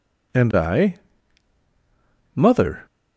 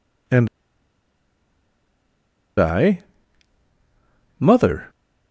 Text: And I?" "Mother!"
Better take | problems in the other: first | pauses between "And" and "I"; strong; at 0.4 s; 2.1 s long

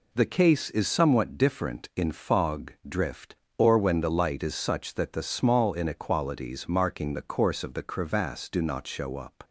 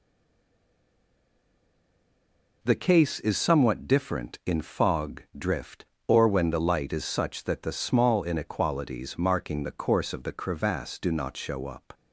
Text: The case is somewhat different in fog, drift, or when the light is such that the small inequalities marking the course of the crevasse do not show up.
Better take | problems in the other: first | stays silent before the first word; strong; until 2.6 s; 2.6 s long

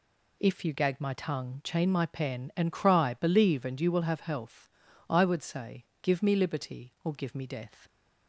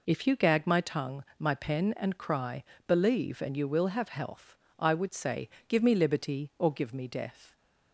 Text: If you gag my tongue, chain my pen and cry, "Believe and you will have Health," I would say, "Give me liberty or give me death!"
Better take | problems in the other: first | skips "chain"; at 1.3 s

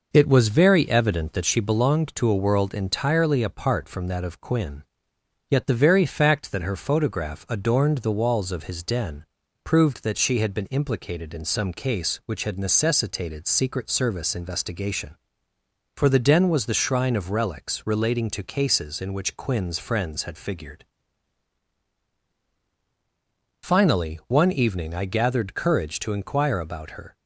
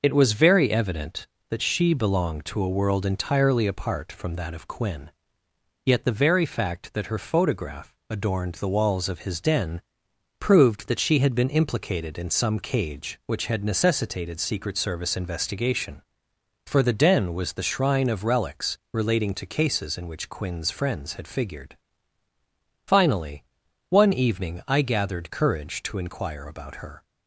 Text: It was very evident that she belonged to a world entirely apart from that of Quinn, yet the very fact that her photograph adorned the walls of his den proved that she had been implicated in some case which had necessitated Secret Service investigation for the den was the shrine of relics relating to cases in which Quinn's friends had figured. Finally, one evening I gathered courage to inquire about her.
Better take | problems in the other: first | pauses between "den" and "proved"; noticeable; at 9.8 s; 0.58 s long; also in the first // says "cage" for "case"; at 12.5 s

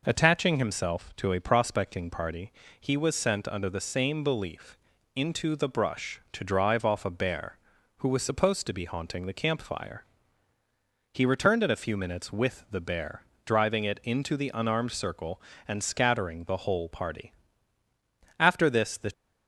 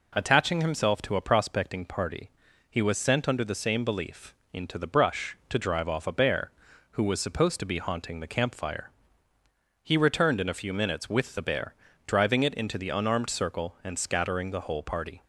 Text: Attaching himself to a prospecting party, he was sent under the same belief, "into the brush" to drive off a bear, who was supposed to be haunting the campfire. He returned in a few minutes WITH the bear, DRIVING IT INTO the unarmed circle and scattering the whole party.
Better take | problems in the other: second | goes on to say "After this the"; noticeable; from 18.3 s on; 0.74 s long

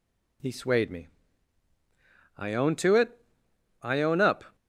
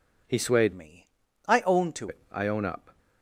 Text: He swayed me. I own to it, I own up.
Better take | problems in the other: first | changes voice from "me" to "to"; from 0.7 to 2.0 s; 1.3 s long

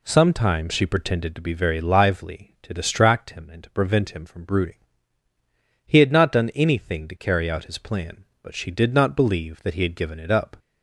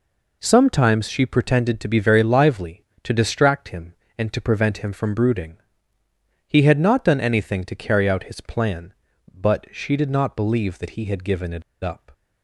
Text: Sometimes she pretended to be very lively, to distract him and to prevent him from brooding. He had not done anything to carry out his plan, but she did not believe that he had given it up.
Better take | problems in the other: first | pauses between "it" and "up"; slight; at 11.6 s; 0.22 s long

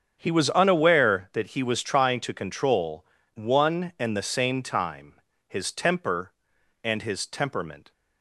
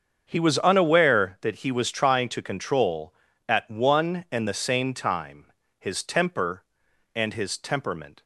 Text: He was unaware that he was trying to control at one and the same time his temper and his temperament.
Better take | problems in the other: second | starts louder than the rest; strong; until 1.2 s; 8 dB; strong in the second // skips "at"; at 3.2 s // pauses between "time" and "his"; slight; at 5.2 s; 0.26 s long; slight in the second

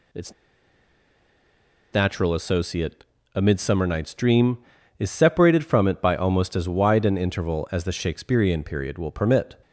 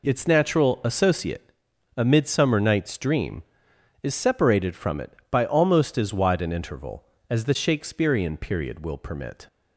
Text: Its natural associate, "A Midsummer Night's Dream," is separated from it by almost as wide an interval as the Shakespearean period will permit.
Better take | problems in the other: second | pauses between "Its" and "natural"; strong; at 0.3 s; 1.5 s long

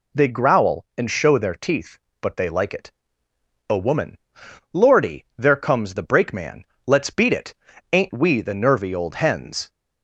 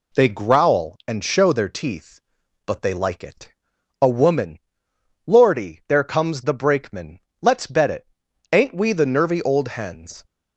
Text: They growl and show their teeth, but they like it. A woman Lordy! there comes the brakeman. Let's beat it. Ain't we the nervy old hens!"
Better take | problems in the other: first | pauses between "woman" and "Lordy"; noticeable; at 4.5 s; 0.66 s long; noticeable in the first // says "bet" for "beat"; at 7.6 s

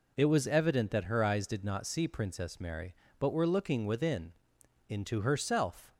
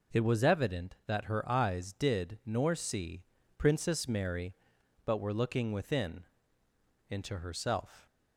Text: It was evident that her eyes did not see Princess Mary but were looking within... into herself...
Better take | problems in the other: first | says "nor" for "not"; at 2.4 s // pauses between "see" and "Princess"; slight; at 3.2 s; 0.36 s long

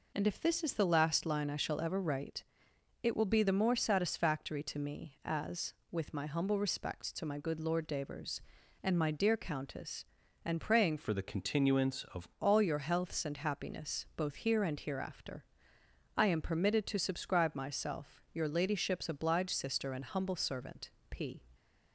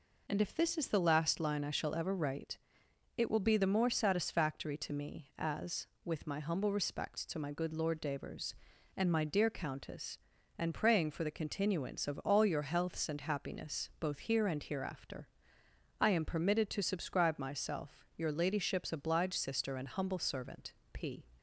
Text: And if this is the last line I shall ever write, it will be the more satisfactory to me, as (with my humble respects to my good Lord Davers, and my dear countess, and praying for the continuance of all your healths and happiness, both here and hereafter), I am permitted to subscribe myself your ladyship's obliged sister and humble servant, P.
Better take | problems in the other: second | changes voice from "for" to "of"; from 10.9 to 12.2 s; 1.3 s long

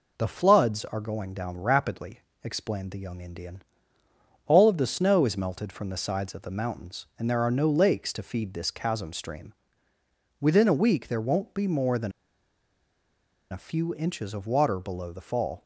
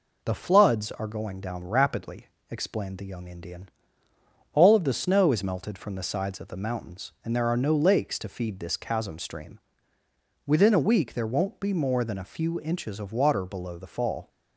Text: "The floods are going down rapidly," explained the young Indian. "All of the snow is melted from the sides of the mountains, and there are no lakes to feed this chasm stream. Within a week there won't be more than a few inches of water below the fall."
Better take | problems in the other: second | pauses between "than" and "a"; strong; at 12.1 s; 1.4 s long

